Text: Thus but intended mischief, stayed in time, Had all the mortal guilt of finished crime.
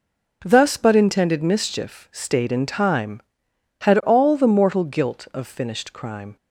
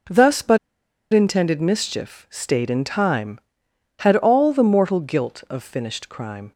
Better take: first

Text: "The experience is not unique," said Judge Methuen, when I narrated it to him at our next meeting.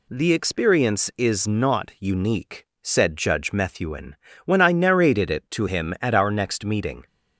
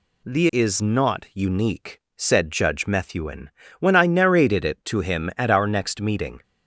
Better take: first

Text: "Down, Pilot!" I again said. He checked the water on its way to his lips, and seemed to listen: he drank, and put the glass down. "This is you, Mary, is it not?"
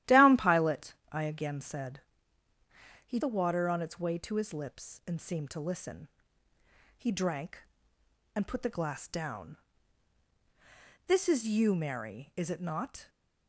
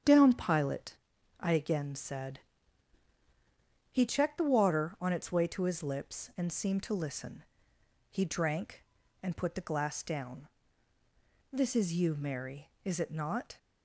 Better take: second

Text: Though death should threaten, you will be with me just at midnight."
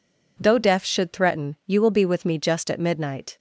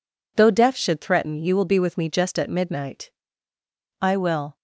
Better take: first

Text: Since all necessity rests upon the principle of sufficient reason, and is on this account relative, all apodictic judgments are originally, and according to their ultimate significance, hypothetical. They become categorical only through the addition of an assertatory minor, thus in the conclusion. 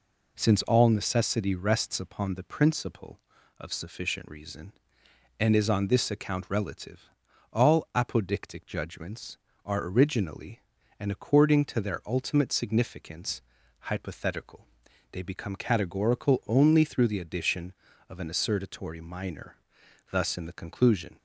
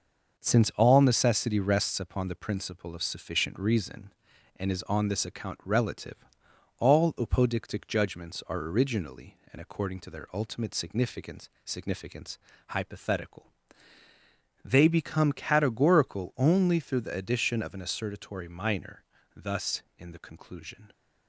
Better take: first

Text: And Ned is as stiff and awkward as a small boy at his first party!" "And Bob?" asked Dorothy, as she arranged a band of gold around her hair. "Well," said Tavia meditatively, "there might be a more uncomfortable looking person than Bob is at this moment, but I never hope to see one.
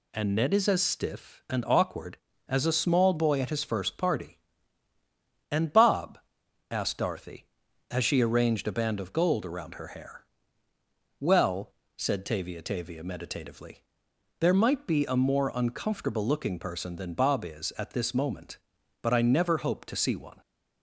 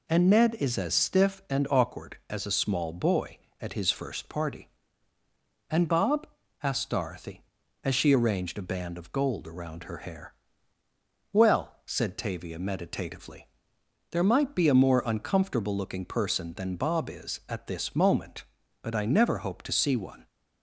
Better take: second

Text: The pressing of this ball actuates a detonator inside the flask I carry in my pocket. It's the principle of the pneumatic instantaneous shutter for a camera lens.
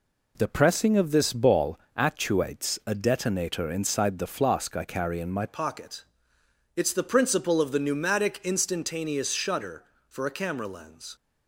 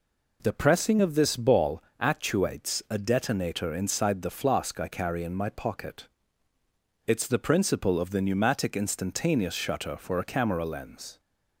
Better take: second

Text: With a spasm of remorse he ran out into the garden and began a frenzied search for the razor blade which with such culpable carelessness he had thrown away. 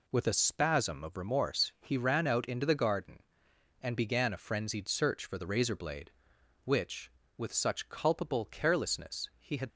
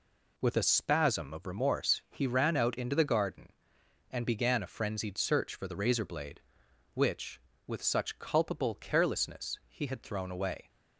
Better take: second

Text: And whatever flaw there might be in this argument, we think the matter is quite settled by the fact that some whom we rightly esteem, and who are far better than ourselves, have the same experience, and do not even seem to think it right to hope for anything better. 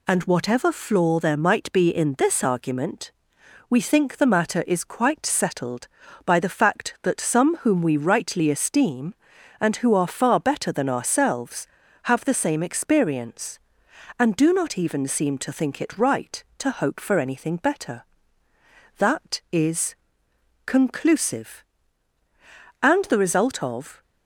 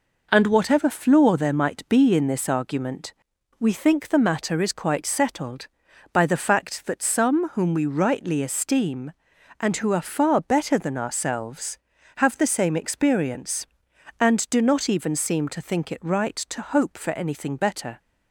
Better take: second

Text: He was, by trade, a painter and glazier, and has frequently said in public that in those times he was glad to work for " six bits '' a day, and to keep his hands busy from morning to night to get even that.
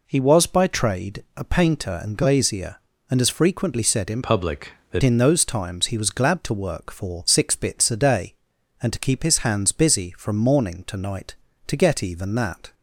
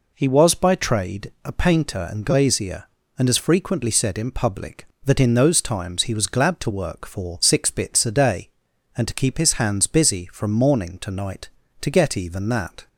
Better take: second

